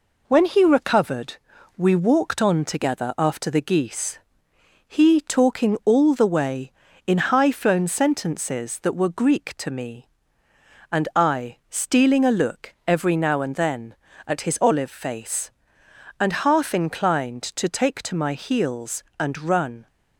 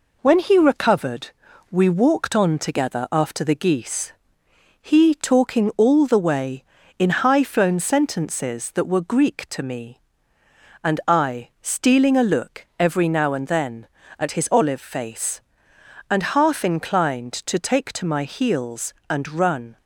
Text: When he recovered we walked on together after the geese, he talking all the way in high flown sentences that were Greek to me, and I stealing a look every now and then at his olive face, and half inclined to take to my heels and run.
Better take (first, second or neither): neither